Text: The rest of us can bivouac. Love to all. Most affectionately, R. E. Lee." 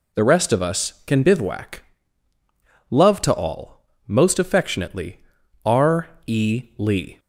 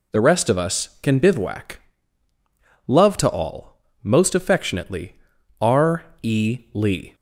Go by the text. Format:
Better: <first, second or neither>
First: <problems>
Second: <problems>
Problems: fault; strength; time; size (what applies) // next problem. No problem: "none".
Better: neither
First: pauses between "R" and "E"; slight; at 6.0 s; 0.18 s long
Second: pauses between "R" and "E"; slight; at 6.0 s; 0.18 s long